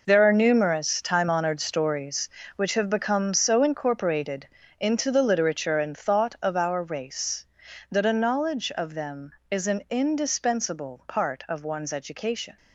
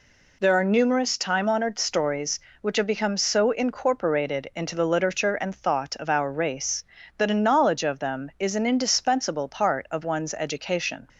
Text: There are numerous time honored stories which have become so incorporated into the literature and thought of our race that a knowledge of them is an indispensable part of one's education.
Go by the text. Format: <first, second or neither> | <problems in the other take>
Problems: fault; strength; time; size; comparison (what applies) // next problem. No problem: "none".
second | gets quieter; strong; throughout; 12 dB // pauses between "incorporated" and "into"; slight; at 4.4 s; 0.32 s long